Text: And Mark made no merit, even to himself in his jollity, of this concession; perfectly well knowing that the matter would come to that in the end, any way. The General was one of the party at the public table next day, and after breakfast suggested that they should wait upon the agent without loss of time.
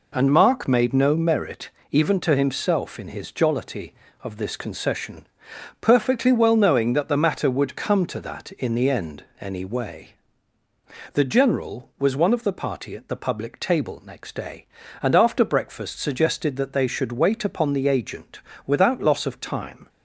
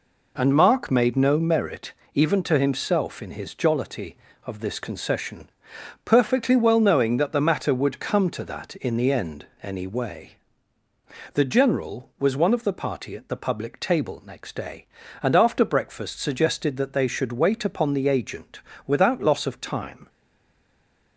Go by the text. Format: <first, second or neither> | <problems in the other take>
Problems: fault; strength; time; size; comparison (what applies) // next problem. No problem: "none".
first | pauses between "agent" and "without"; slight; at 18.6 s; 0.26 s long; slight in the first // stays silent after the last word; from 20.0 s on; 1.1 s long